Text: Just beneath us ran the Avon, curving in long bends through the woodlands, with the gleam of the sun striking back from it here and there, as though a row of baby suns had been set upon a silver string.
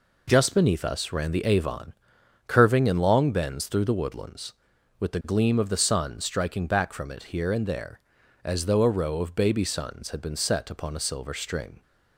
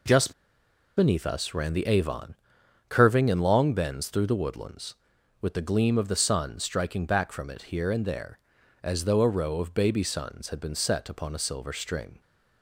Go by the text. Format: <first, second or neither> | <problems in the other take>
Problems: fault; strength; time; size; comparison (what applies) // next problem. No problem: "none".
first | pauses between "Just" and "beneath"; noticeable; at 0.3 s; 0.66 s long